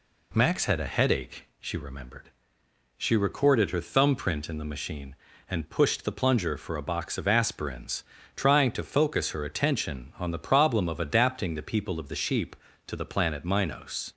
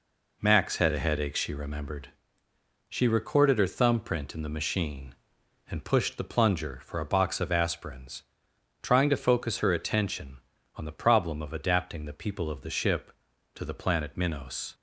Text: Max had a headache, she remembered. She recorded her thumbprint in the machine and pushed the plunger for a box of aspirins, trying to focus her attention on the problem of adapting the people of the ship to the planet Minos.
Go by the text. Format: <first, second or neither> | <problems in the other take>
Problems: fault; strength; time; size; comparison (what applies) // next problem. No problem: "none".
second | says "sheep" for "ship"; at 12.1 s